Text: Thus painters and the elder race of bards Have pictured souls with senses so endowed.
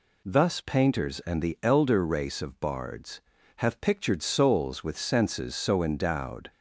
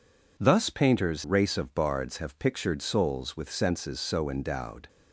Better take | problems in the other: first | skips "and the elder"; at 1.2 s

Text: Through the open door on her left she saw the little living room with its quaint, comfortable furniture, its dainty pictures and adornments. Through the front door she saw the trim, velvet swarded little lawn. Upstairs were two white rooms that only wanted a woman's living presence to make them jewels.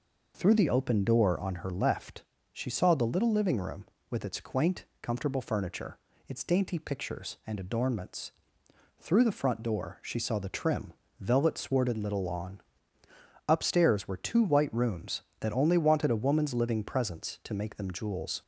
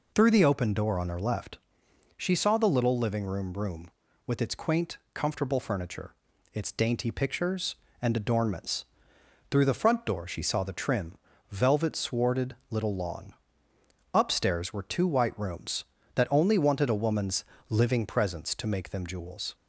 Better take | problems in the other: first | pauses between "left" and "she"; noticeable; at 1.5 s; 0.60 s long; slight in the first // says "room" twice; at 3.5 s // pauses between "woman's" and "living"; slight; at 17.4 s; 0.28 s long

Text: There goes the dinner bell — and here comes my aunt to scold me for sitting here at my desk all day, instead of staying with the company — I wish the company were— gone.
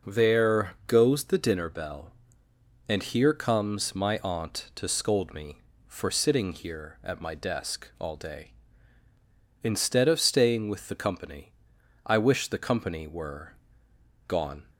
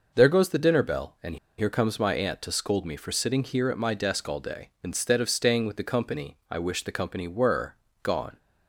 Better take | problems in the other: first | pauses between "and" and "here"; slight; at 1.3 s; 0.21 s long

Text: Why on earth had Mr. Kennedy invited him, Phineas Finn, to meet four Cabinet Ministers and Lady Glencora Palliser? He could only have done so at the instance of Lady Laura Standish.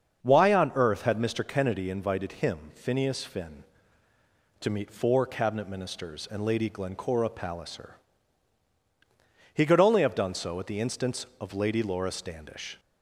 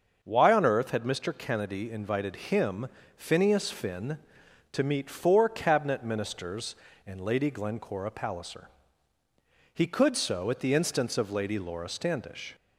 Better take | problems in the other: first | starts louder than the rest; until 1.2 s; 6.5 dB; also in the first // skips "only have done"; at 10.1 s

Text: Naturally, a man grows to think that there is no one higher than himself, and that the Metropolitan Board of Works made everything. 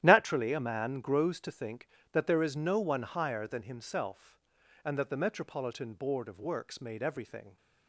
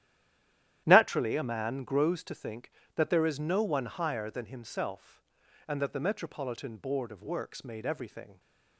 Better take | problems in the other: first | stays silent before the first word; slight; until 0.8 s; 0.8 s long // starts louder than the rest; strong; until 1.8 s; 12 dB; strong in the first

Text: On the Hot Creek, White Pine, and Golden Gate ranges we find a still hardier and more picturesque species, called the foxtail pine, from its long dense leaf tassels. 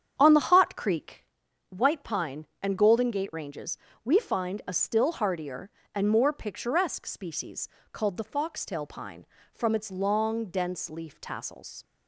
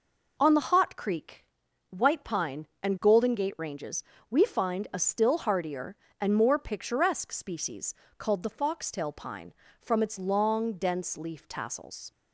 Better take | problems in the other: second | starts louder than the rest; strong; until 1.2 s; 8.5 dB // pauses between "ranges" and "we"; slight; at 3.7 s; 0.28 s long; slight in the second

